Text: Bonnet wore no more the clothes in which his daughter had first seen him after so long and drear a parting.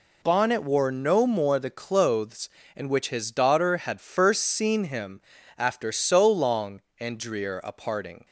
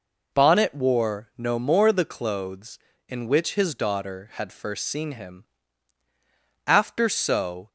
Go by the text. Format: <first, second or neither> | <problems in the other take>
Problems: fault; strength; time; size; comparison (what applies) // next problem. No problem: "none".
first | pauses between "him" and "after"; at 5.4 s; 1.2 s long; slight in the first // stops before "long and drear a parting"; at 7.6 s